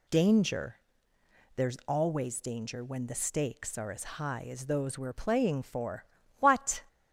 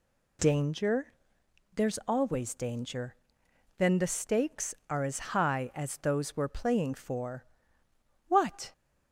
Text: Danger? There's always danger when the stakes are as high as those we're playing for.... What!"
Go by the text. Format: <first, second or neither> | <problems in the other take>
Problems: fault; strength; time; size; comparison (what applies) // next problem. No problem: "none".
first | says "then" for "when"; at 3.7 s